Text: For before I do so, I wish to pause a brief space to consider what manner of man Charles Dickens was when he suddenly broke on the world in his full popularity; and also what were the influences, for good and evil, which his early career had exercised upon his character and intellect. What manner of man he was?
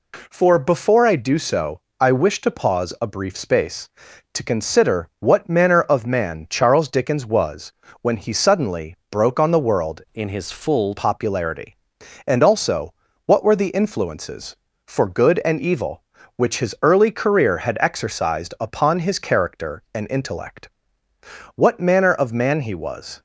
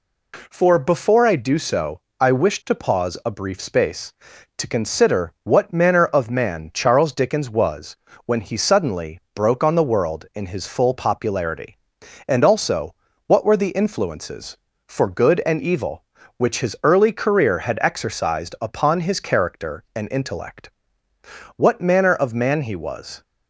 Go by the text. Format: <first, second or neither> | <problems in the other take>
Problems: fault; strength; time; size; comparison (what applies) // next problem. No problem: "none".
second | pauses between "was" and "when"; slight; at 7.7 s; 0.28 s long; slight in the second // pauses between "suddenly" and "broke"; slight; at 8.9 s; 0.16 s long; slight in the second // changes voice from "in" to "full"; from 10.1 to 10.9 s; 0.8 s long // pauses between "also" and "what"; slight; at 12.9 s; 0.32 s long; slight in the second